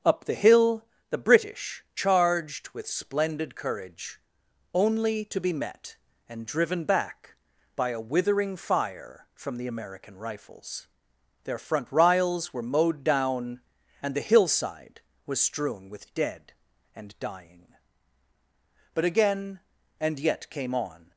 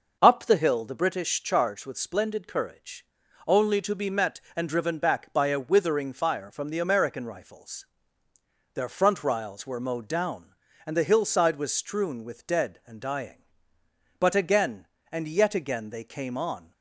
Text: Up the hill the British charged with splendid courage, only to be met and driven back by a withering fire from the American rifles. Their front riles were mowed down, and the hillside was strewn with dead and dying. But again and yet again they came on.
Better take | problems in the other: second | starts louder than the rest; until 1.2 s; 6.5 dB // pauses between "hill" and "the"; slight; at 0.8 s; 0.26 s long // skips "again they"; at 20.4 s

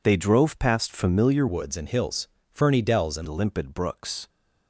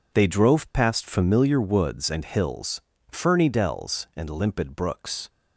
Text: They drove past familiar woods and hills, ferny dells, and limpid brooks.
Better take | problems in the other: second | changes voice from "woods" to "and"; from 1.4 to 3.2 s; 1.8 s long

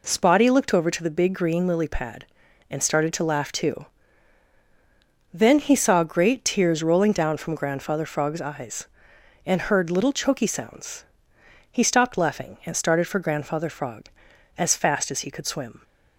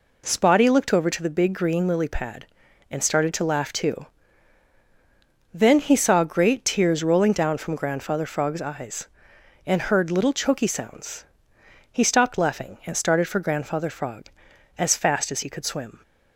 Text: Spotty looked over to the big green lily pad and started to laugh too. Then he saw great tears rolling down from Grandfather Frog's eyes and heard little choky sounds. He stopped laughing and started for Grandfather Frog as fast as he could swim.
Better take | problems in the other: neither | none

